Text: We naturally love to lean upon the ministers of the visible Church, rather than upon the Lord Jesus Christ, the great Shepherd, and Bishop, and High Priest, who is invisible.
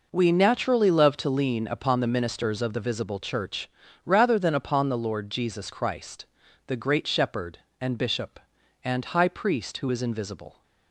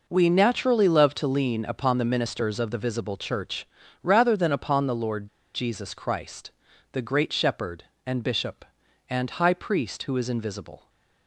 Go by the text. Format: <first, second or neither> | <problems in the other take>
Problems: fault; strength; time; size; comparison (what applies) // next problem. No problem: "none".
first | pauses between "Lord" and "Jesus"; slight; at 5.2 s; 0.27 s long